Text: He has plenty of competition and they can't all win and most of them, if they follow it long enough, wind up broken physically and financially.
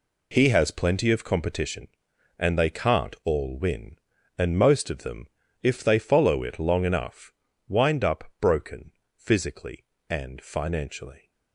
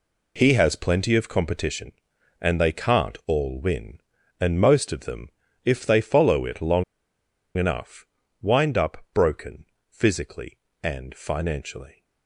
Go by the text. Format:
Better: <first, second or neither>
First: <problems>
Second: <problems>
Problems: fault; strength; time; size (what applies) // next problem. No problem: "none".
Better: first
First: pauses between "up" and "broken"; slight; at 8.2 s; 0.16 s long // pauses between "broken" and "physically"; slight; at 8.9 s; 0.26 s long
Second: pauses between "long" and "enough"; noticeable; at 6.8 s; 0.73 s long // pauses between "up" and "broken"; slight; at 8.9 s; 0.16 s long // pauses between "broken" and "physically"; slight; at 9.6 s; 0.26 s long